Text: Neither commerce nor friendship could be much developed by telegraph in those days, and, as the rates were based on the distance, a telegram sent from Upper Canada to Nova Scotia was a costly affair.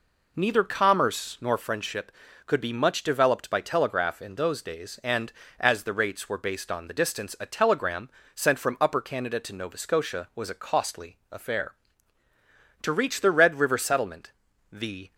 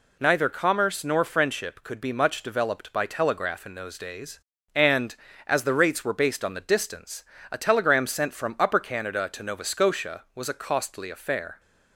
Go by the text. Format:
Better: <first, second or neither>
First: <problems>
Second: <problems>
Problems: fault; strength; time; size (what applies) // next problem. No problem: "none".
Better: second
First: pauses between "telegram" and "sent"; slight; at 8.1 s; 0.24 s long // goes on to say "To reach the Red River Settlement the"; strong; from 12.8 s on; 2.3 s long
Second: none